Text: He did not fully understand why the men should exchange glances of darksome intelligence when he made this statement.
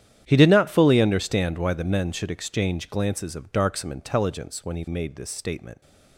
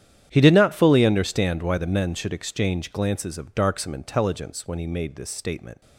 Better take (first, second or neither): neither